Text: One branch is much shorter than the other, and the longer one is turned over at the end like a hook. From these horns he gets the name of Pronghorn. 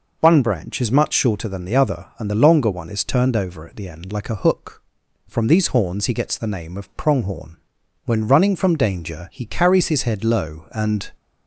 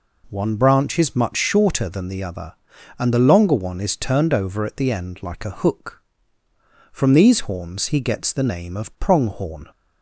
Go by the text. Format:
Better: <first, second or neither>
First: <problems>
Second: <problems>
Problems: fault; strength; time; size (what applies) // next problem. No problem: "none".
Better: second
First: goes on to say "When running from danger he carries his head low and"; strong; from 8.0 s on; 3.0 s long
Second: none